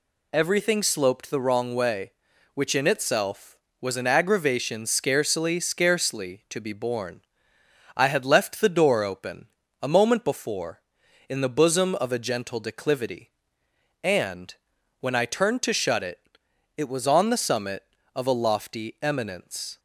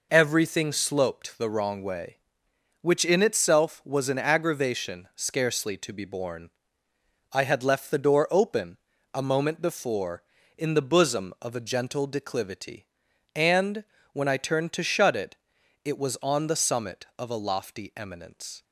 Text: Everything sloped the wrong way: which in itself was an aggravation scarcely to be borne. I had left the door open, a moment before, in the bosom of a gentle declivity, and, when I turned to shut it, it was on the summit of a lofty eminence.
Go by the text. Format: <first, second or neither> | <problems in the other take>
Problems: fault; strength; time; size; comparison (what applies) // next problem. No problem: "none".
second | says "scarcely" twice; at 5.5 s